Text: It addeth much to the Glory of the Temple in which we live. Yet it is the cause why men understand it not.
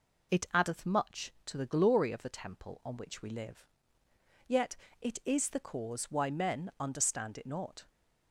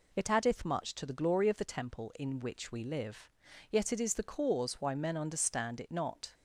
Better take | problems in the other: second | says "on" for "in"; at 2.8 s // pauses between "Yet" and "it"; slight; at 4.7 s; 0.26 s long

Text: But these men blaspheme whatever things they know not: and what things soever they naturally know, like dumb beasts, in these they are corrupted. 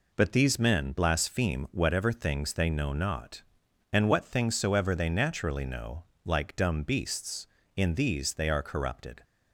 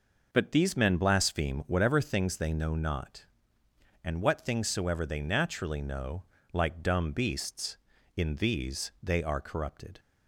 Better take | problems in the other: neither | none

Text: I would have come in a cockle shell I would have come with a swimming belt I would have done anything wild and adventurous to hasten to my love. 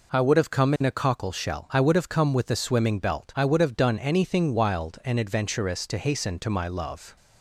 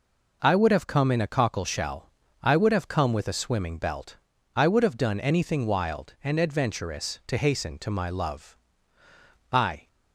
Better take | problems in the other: first | pauses between "shell" and "I"; slight; at 2.0 s; 0.32 s long // pauses between "belt" and "I"; at 4.1 s; 0.38 s long // goes on to say "I"; slight; from 9.5 s on; 0.36 s long

